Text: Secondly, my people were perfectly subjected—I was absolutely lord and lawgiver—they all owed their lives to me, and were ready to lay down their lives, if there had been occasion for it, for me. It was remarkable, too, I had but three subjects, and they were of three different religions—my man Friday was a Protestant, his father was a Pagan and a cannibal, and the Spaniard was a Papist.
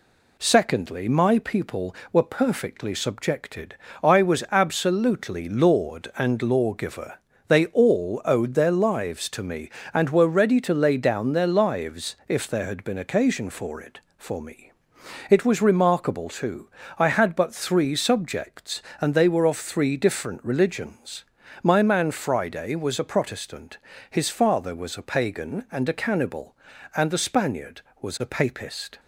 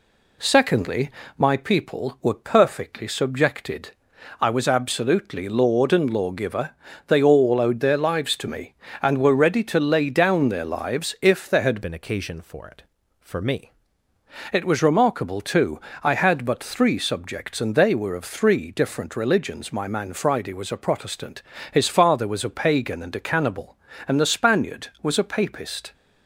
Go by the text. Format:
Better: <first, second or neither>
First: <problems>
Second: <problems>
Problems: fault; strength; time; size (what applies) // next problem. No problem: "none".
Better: first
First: none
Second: changes voice from "been" to "me"; from 11.8 to 13.7 s; 1.9 s long